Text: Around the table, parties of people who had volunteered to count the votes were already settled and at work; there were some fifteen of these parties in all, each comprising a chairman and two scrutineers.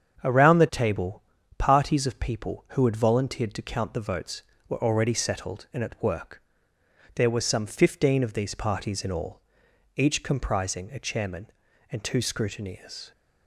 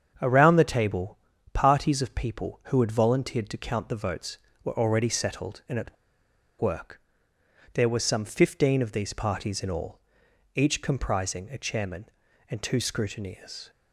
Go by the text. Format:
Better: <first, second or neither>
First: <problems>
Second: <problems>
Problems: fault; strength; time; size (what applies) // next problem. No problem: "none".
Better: first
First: starts louder than the rest; strong; until 1.6 s; 7.5 dB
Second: starts louder than the rest; strong; until 1.5 s; 7.5 dB // pauses between "at" and "work"; noticeable; at 5.9 s; 0.66 s long